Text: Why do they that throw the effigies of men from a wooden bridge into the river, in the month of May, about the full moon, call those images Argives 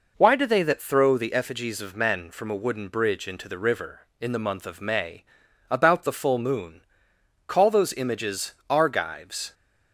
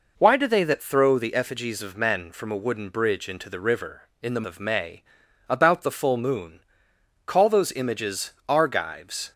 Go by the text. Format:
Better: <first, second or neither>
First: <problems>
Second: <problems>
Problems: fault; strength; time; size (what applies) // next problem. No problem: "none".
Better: first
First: pauses between "images" and "Argives"; slight; at 8.5 s; 0.16 s long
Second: skips "month"; at 4.4 s // pauses between "images" and "Argives"; slight; at 8.3 s; 0.16 s long